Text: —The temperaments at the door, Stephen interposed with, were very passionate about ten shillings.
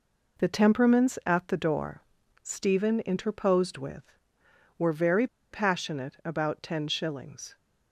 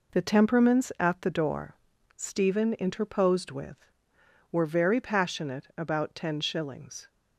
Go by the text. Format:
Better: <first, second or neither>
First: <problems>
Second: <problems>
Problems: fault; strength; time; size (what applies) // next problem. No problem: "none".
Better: second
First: pauses between "very" and "passionate"; slight; at 5.2 s; 0.25 s long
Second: none